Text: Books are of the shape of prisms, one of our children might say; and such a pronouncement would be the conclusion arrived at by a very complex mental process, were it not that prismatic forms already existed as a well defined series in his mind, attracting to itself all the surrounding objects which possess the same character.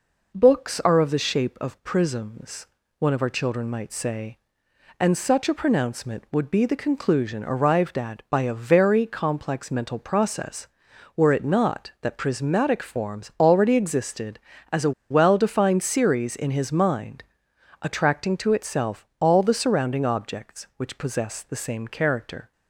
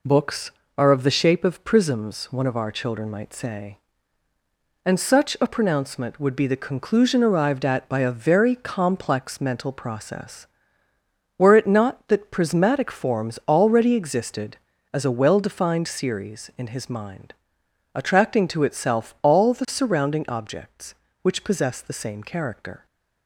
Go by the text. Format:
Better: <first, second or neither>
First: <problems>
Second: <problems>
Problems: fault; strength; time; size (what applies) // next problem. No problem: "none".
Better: second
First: pauses between "a" and "well"; slight; at 14.9 s; 0.19 s long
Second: none